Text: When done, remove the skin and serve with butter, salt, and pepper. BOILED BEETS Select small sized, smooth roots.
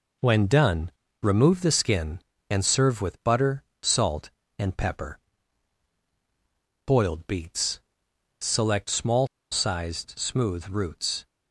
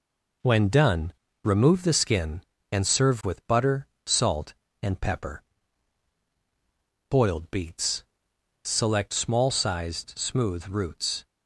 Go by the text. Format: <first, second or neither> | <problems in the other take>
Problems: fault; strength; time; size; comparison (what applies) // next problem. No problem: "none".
second | pauses between "BEETS" and "Select"; noticeable; at 7.7 s; 0.62 s long; noticeable in the second // pauses between "small" and "sized"; slight; at 9.2 s; 0.24 s long